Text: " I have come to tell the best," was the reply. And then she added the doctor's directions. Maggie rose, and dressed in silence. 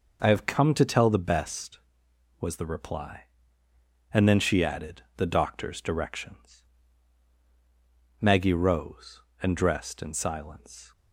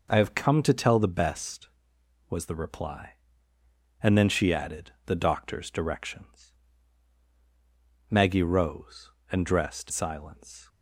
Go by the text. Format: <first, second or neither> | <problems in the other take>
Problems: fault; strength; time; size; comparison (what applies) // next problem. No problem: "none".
first | skips "in"; at 9.8 s